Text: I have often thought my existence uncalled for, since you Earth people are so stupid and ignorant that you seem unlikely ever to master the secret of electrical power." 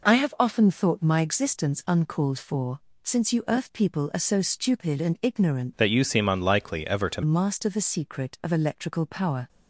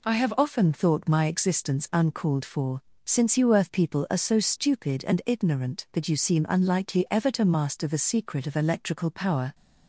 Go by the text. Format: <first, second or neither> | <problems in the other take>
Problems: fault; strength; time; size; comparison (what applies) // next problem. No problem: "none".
second | changes voice from "that" to "to"; from 5.7 to 7.2 s; 1.5 s long